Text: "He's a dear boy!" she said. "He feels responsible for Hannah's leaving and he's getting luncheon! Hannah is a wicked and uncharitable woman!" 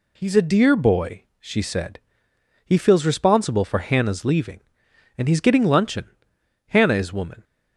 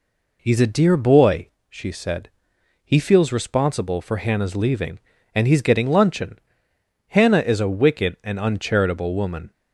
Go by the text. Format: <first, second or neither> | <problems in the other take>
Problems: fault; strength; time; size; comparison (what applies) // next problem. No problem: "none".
second | skips "a wicked and uncharitable"; at 7.1 s